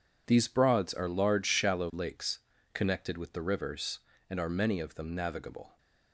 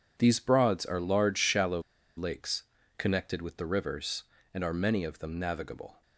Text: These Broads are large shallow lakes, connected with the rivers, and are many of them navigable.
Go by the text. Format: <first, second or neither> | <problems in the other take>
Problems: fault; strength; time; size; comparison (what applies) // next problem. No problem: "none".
first | pauses between "shallow" and "lakes"; slight; at 1.8 s; 0.35 s long